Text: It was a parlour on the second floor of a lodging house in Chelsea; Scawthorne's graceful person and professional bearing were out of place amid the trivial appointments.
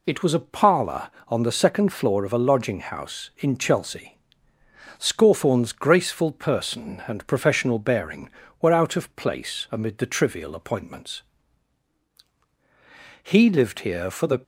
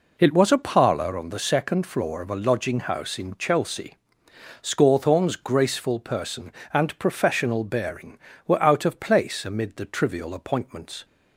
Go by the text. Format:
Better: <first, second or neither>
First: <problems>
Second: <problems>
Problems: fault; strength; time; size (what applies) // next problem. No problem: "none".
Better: second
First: goes on to say "He lived here for the"; noticeable; from 13.2 s on; 1.1 s long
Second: none